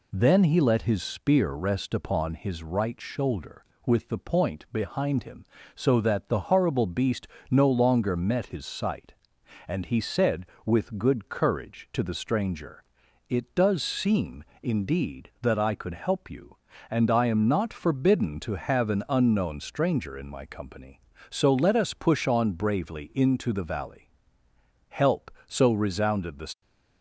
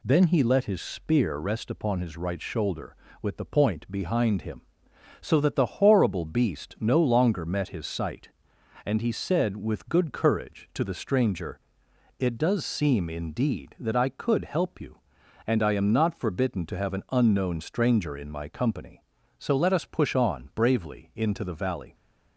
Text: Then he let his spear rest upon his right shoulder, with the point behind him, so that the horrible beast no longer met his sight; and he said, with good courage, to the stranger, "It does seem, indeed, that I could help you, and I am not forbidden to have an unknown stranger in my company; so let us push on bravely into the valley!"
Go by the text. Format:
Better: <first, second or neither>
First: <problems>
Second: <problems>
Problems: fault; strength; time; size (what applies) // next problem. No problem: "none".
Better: second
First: pauses between "beast" and "no"; slight; at 7.2 s; 0.20 s long // goes on to say "Help so resounded the"; strong; from 24.8 s on; 1.7 s long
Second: none